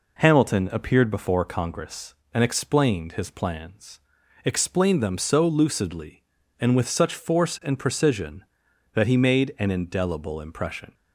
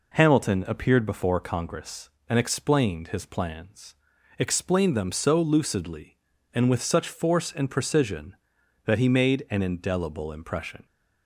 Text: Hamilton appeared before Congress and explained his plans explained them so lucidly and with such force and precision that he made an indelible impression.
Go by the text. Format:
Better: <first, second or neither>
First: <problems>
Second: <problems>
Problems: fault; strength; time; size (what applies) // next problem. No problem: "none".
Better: neither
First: pauses between "plans" and "explained"; noticeable; at 3.9 s; 0.46 s long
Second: pauses between "plans" and "explained"; at 3.9 s; 0.44 s long